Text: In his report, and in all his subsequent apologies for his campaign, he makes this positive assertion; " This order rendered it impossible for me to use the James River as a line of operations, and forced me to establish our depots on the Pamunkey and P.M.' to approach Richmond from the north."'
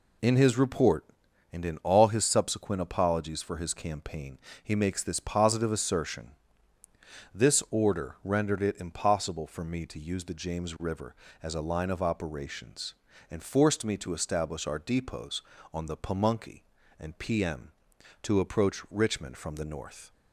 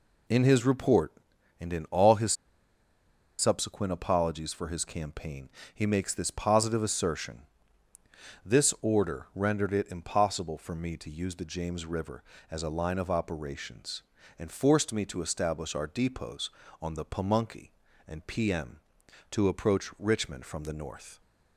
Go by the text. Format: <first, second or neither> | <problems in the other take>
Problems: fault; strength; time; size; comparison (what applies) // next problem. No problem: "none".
first | pauses between "his" and "subsequent"; at 2.3 s; 1.0 s long